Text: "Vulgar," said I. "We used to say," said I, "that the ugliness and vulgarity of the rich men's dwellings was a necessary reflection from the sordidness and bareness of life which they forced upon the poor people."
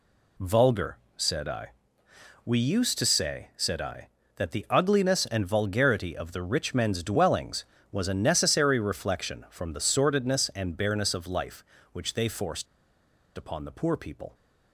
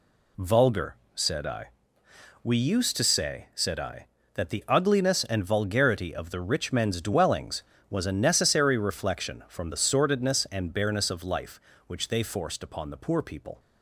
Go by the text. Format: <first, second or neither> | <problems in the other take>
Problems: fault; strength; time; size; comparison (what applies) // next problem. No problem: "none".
second | pauses between "forced" and "upon"; noticeable; at 12.6 s; 0.71 s long